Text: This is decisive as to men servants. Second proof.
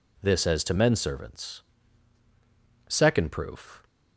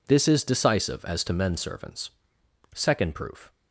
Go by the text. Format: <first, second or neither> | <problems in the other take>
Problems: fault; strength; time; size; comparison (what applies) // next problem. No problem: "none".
second | skips "is decisive"; at 0.4 s